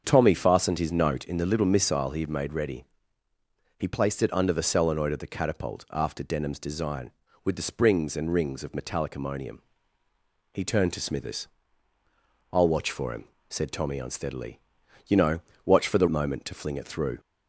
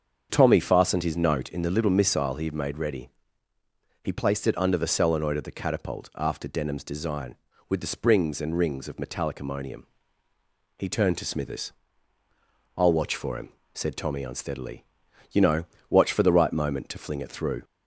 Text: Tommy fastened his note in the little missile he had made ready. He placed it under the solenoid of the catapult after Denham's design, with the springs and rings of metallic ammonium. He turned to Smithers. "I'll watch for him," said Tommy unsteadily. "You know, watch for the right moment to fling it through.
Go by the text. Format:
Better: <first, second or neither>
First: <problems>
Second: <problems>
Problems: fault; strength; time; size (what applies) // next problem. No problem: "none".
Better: second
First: starts louder than the rest; until 1.0 s; 7 dB // skips "right"; at 16.0 s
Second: starts louder than the rest; until 1.3 s; 7 dB